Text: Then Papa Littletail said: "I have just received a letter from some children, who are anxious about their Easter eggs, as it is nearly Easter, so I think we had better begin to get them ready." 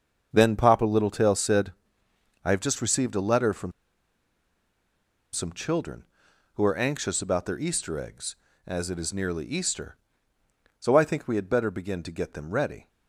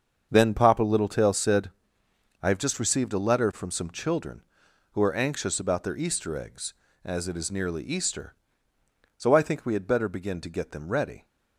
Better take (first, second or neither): second